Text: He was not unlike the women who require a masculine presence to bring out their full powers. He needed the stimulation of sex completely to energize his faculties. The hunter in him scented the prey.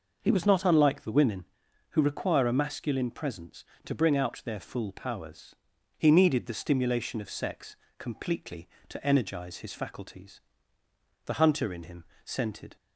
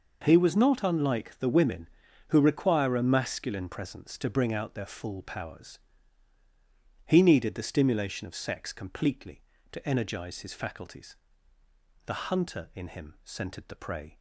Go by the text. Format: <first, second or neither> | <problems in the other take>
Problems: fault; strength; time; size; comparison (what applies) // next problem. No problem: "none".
second | pauses between "sex" and "completely"; slight; at 7.7 s; 0.22 s long // pauses between "him" and "scented"; slight; at 12.0 s; 0.20 s long // stops before "the prey"; at 12.7 s